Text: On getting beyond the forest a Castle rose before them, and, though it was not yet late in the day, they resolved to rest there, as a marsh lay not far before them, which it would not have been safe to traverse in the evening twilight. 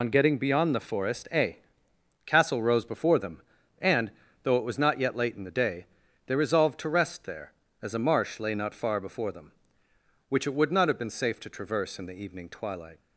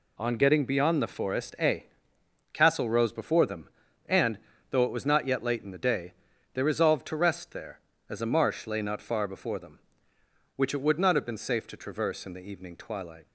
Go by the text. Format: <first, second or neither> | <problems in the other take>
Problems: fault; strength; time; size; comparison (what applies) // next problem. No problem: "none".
second | loses the start of "On"; at 0.0 s; 90 ms // pauses between "a" and "Castle"; noticeable; at 1.5 s; 0.68 s long; noticeable in the second